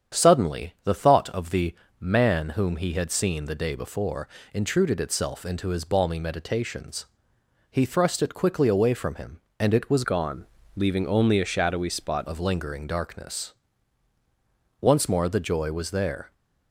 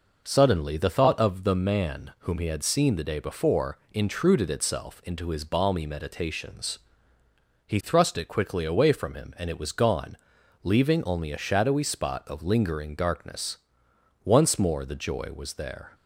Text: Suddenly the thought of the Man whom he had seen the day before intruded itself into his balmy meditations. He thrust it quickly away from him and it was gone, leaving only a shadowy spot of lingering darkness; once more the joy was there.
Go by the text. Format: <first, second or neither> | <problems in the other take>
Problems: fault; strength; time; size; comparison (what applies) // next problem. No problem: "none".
second | starts louder than the rest; strong; until 1.2 s; 8.5 dB // pauses between "the" and "Man"; slight; at 1.7 s; 0.24 s long // pauses between "before" and "intruded"; slight; at 4.2 s; 0.26 s long; slight in the second // changes voice from "gone" to "spot"; from 10.0 to 12.2 s; 2.2 s long